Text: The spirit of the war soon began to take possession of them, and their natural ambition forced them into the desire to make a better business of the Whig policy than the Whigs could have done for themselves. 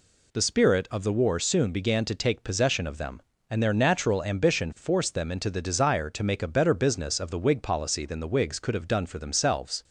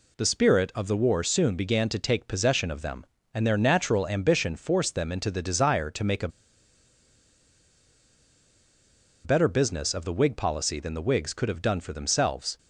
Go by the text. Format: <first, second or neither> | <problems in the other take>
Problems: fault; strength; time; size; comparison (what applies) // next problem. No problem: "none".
first | pauses between "a" and "better"; strong; at 6.2 s; 2.9 s long